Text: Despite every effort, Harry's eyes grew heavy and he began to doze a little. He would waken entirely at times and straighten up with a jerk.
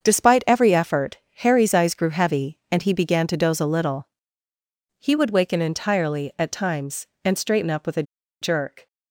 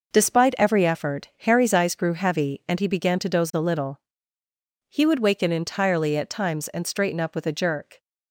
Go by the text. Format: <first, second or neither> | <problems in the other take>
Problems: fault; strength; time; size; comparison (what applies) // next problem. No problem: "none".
second | starts louder than the rest; until 1.0 s; 7 dB // pauses between "a" and "jerk"; at 8.0 s; 0.38 s long